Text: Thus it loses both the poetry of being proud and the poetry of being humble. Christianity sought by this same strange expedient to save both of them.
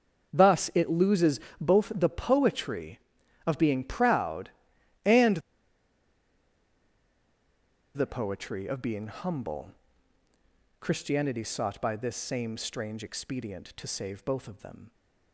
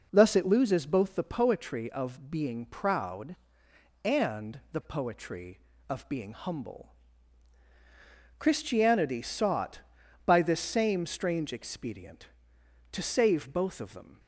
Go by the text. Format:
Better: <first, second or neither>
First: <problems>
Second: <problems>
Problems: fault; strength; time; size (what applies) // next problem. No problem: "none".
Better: second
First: starts louder than the rest; until 1.3 s; 7 dB // pauses between "loses" and "both"; slight; at 1.4 s; 0.20 s long // pauses between "and" and "the"; strong; at 5.3 s; 2.5 s long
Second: none